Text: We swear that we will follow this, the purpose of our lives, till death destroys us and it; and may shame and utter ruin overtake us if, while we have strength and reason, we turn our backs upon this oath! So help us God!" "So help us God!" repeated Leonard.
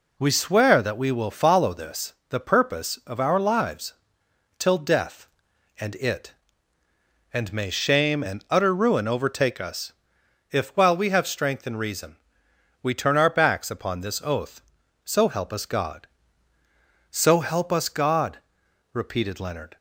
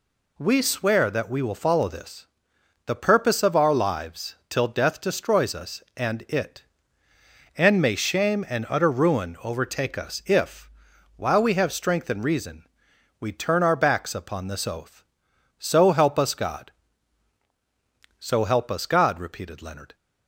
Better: second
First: skips "destroys us"; at 5.5 s // pauses between "us" and "if"; noticeable; at 9.9 s; 0.58 s long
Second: none

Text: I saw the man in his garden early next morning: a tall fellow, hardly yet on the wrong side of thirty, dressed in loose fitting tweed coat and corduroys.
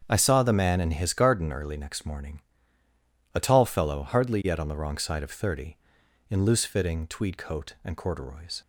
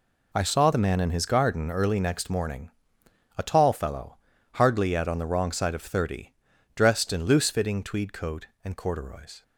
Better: second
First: starts louder than the rest; strong; until 1.1 s; 7.5 dB // skips "dressed"; at 6.0 s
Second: none

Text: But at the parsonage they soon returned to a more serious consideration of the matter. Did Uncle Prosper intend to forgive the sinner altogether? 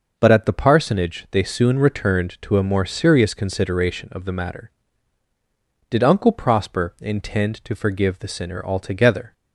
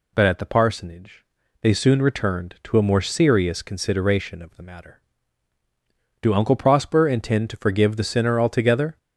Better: first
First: none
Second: pauses between "parsonage" and "they"; at 1.2 s; 0.38 s long // says "Do" for "Did"; at 6.2 s

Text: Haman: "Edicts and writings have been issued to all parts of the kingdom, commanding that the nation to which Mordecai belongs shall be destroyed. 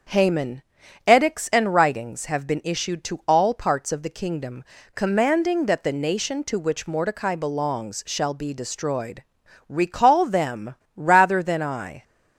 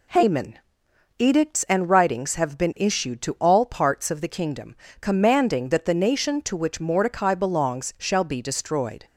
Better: second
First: starts louder than the rest; until 1.5 s; 6.5 dB // goes on to say "Recall them rather than I"; strong; from 9.6 s on; 2.3 s long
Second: none

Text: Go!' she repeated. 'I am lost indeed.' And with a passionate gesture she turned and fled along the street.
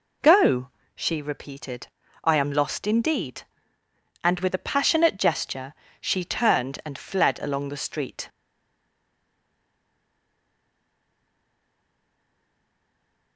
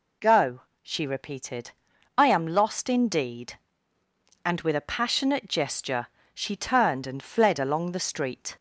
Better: second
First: pauses between "gesture" and "she"; slight; at 5.7 s; 0.26 s long // stays silent after the last word; strong; from 8.2 s on; 5.1 s long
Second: pauses between "gesture" and "she"; slight; at 6.0 s; 0.26 s long

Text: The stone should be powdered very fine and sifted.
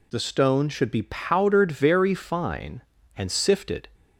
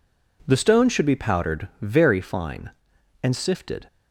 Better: neither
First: none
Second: none

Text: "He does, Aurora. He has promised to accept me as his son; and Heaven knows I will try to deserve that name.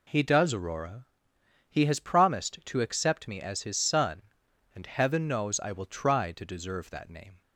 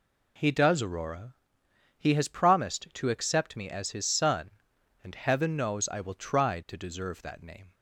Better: neither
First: none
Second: none

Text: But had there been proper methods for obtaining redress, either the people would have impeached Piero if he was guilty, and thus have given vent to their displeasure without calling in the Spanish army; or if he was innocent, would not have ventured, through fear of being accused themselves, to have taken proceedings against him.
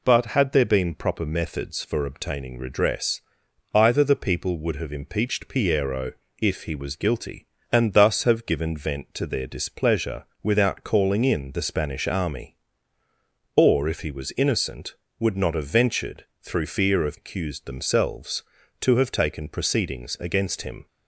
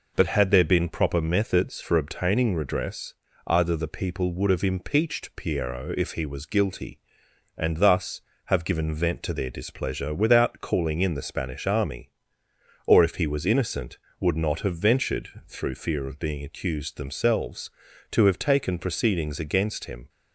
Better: second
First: pauses between "Piero" and "if"; slight; at 6.1 s; 0.28 s long // pauses between "displeasure" and "without"; slight; at 10.2 s; 0.18 s long // skips "being"; at 17.1 s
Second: none

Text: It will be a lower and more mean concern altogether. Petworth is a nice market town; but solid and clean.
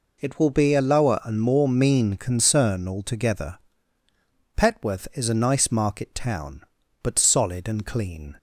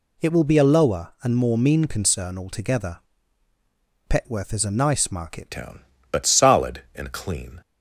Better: first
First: none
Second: changes voice at "town"; from 5.5 s on; 2.1 s long

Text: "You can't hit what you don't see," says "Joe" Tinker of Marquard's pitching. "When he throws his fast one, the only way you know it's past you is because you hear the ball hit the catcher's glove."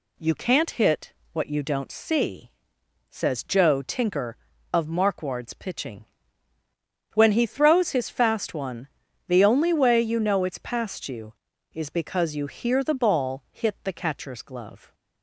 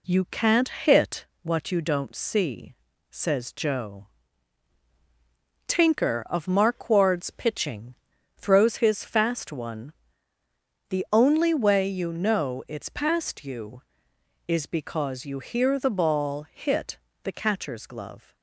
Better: first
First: pauses between "hit" and "what"; slight; at 1.1 s; 0.22 s long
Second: pauses between "hit" and "what"; slight; at 1.2 s; 0.16 s long // pauses between "Joe" and "Tinker"; strong; at 4.0 s; 1.6 s long // skips "When he"; at 8.1 s // pauses between "hit" and "the"; slight; at 16.9 s; 0.24 s long

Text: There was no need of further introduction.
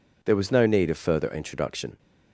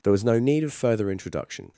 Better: neither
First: none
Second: none

